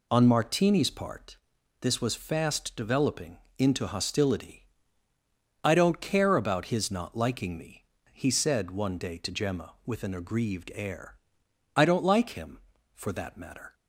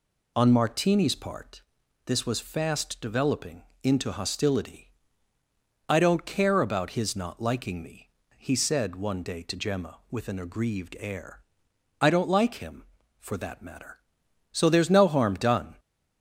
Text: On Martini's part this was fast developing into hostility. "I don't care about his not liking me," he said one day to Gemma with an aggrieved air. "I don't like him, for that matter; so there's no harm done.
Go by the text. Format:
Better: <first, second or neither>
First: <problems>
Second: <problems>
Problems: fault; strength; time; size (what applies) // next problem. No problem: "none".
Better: second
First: pauses between "part" and "this"; noticeable; at 1.3 s; 0.46 s long // pauses between "developing" and "into"; slight; at 3.3 s; 0.22 s long // stops before "so there's no harm done"; at 13.7 s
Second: pauses between "part" and "this"; noticeable; at 1.6 s; 0.46 s long // pauses between "developing" and "into"; slight; at 3.6 s; 0.22 s long